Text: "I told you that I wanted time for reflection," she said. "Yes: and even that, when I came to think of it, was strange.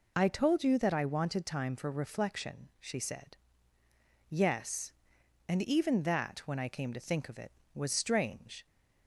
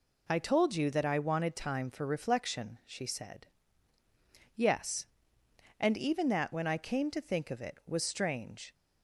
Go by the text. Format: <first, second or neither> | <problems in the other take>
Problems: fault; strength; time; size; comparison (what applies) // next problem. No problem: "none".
neither | none